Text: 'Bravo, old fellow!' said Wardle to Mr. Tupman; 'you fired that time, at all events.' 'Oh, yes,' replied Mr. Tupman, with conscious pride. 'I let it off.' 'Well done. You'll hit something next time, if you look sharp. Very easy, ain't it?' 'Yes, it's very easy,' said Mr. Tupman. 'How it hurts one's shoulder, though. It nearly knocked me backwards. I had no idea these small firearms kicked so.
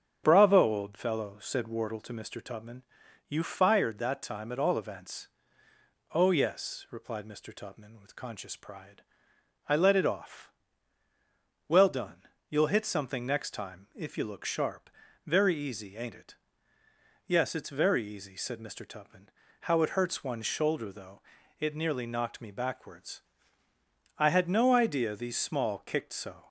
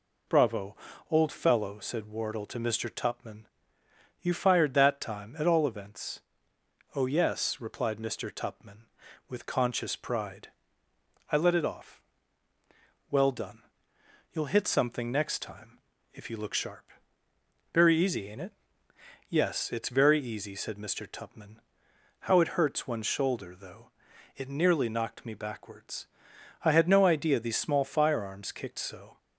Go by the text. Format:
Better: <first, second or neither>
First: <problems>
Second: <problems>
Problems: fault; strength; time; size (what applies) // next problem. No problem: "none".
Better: second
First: starts louder than the rest; strong; until 1.2 s; 8 dB // skips "firearms"; at 25.8 s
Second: none